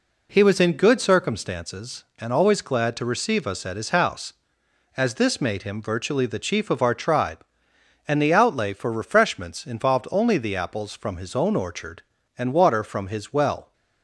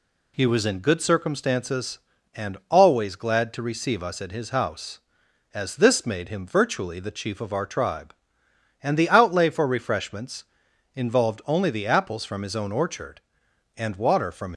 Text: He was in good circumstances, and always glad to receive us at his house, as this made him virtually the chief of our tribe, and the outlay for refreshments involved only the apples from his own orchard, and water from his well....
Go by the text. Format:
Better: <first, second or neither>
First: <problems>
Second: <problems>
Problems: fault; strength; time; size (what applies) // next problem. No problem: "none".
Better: first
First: none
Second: pauses between "refreshments" and "involved"; noticeable; at 10.4 s; 0.50 s long // stops before "his well"; at 14.5 s